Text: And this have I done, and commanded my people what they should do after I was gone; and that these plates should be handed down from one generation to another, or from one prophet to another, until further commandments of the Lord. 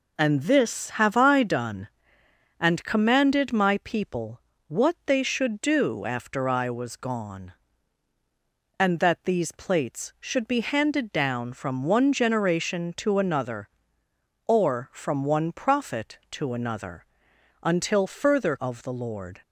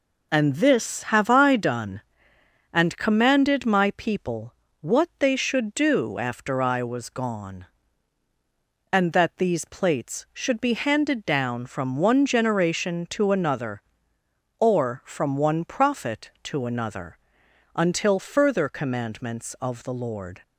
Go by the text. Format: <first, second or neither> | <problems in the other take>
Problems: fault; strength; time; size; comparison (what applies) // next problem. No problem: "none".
second | pauses between "people" and "what"; slight; at 4.3 s; 0.28 s long; slight in the second // skips "commandments"; at 18.5 s